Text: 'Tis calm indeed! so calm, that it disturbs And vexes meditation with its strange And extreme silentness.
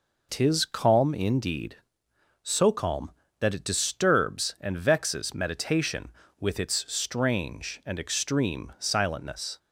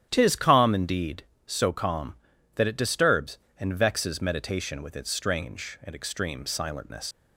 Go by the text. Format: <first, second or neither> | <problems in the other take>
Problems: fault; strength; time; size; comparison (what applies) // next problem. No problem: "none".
first | starts louder than the rest; strong; until 1.1 s; 10.5 dB // leaves "silentness" unfinished; at 7.1 s; 75 ms